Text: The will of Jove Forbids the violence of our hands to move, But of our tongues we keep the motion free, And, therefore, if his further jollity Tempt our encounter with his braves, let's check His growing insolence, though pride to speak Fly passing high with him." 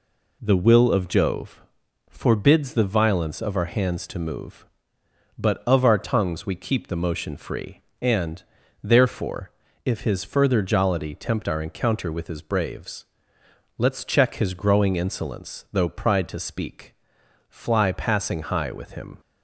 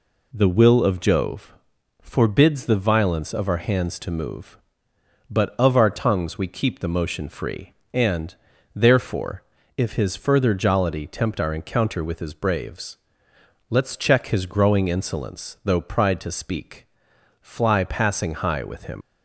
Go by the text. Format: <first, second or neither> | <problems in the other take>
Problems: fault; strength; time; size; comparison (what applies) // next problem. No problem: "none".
first | pauses between "Jove" and "Forbids"; noticeable; at 1.5 s; 0.48 s long; noticeable in the first // pauses between "speak" and "Fly"; noticeable; at 16.8 s; 0.54 s long; noticeable in the first // leaves "him" unfinished; at 19.0 s; 110 ms